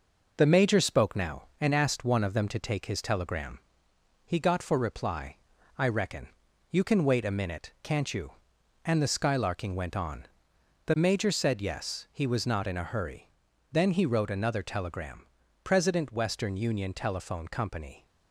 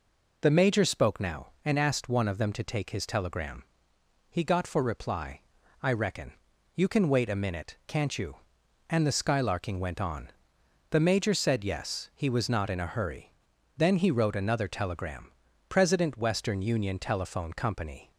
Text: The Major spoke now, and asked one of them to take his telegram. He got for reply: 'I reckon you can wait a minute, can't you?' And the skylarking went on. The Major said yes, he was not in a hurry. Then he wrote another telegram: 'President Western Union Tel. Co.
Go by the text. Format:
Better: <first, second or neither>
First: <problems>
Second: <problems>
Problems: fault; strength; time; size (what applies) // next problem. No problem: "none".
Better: second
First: gets quieter; noticeable; throughout; 4.5 dB // pauses between "reckon" and "you"; at 6.2 s; 0.44 s long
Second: pauses between "reckon" and "you"; at 6.3 s; 0.44 s long